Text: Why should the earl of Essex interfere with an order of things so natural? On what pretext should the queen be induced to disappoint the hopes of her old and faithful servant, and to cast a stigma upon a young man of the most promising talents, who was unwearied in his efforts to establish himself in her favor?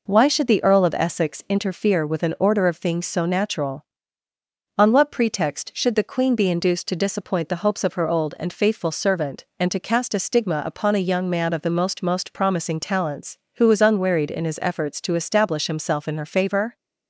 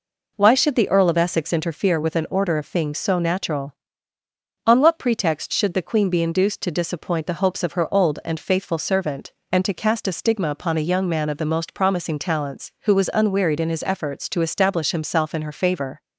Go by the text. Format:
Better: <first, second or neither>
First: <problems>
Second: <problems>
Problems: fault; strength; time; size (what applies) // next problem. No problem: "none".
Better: second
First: says "most" twice; at 12.0 s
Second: none